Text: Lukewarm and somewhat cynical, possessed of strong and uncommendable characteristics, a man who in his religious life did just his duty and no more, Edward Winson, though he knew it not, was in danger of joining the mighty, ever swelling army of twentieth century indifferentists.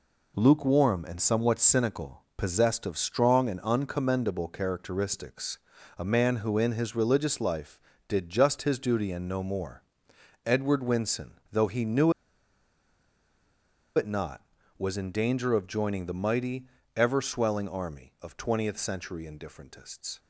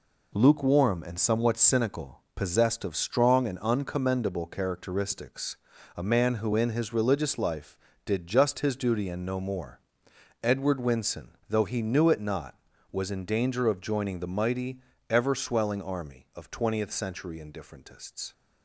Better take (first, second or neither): second